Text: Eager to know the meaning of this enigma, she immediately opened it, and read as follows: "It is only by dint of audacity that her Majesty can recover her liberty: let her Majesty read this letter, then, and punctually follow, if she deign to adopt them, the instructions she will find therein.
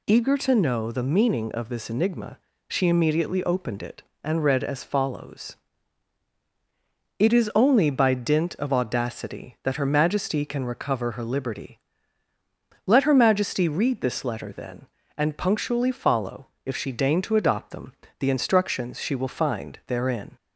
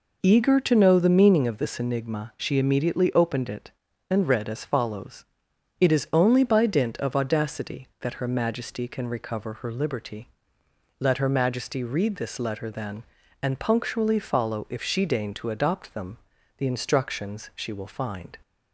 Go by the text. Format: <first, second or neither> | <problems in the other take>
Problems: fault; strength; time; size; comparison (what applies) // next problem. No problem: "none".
first | stops before "therein"; at 18.4 s